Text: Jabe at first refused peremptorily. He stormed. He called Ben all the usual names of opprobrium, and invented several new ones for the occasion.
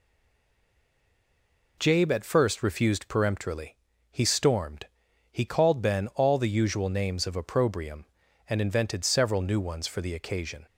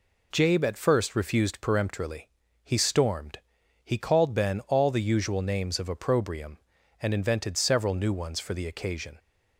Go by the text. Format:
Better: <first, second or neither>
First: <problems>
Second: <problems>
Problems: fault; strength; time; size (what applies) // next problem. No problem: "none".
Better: second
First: stays silent before the first word; noticeable; until 1.7 s; 1.7 s long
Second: none